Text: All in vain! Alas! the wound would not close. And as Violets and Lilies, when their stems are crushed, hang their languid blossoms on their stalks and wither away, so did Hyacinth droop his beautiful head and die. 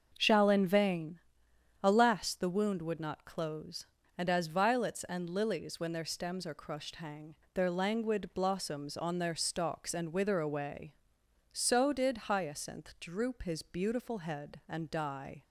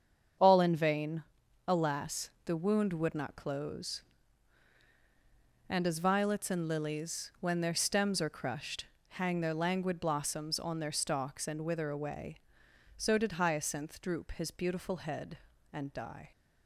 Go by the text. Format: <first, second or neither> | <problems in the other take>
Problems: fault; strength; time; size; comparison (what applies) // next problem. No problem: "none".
second | starts louder than the rest; until 1.1 s; 6.5 dB; strong in the second // says "Shall" for "All"; at 0.1 s // pauses between "hang" and "their"; slight; at 7.3 s; 0.20 s long